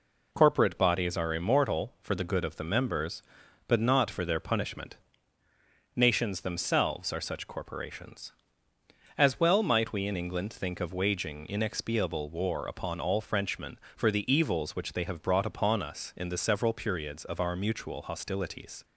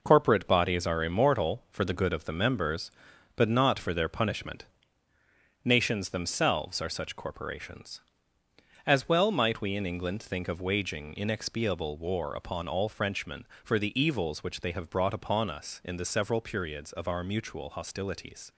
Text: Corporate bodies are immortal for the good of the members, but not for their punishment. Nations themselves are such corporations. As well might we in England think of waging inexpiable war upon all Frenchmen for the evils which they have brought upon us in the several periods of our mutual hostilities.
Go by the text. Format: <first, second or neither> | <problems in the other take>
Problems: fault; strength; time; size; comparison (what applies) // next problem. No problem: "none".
first | gets quieter; throughout; 7 dB